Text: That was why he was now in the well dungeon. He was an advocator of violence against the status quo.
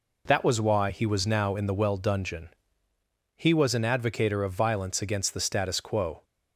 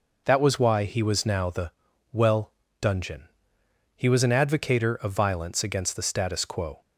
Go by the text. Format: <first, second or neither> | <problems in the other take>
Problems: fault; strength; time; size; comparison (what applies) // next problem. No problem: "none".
first | skips "in"; at 1.4 s // pauses between "the" and "well"; at 1.6 s; 0.42 s long // pauses between "well" and "dungeon"; slight; at 2.5 s; 0.28 s long